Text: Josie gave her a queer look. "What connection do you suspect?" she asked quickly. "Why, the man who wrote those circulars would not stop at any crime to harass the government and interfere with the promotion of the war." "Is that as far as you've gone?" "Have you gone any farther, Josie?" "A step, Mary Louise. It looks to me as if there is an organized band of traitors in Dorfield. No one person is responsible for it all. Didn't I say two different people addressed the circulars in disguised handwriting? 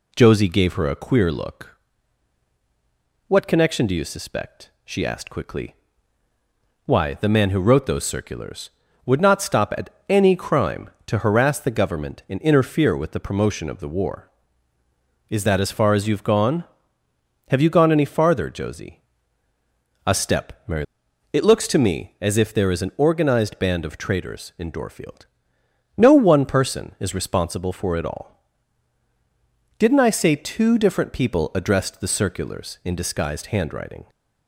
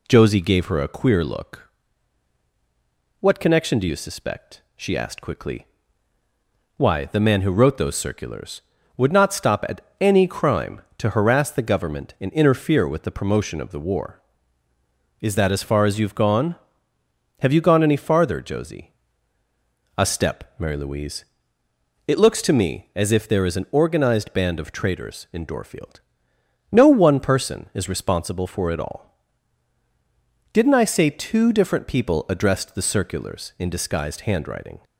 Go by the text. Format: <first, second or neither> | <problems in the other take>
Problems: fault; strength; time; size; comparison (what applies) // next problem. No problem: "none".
second | pauses between "at" and "any"; slight; at 9.8 s; 0.22 s long; slight in the second // skips "Louise"; at 21.0 s